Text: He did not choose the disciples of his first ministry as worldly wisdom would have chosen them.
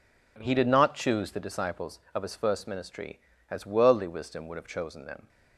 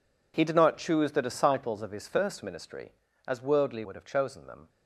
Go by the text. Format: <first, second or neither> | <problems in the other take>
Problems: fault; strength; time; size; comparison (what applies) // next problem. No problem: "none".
first | skips "wisdom"; at 3.8 s